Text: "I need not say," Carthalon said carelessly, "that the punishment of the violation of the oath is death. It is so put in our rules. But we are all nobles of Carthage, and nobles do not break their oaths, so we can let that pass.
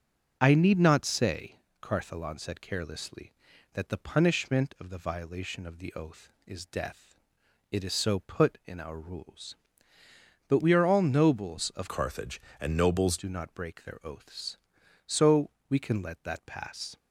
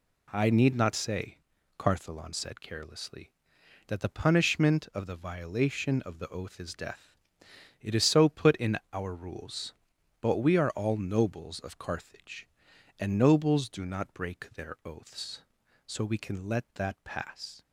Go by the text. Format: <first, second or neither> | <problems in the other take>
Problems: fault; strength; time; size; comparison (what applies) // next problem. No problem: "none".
second | starts louder than the rest; until 1.4 s; 6.5 dB // changes voice from "Carthage" to "nobles"; from 11.8 to 13.1 s; 1.3 s long // pauses between "so" and "we"; slight; at 15.5 s; 0.18 s long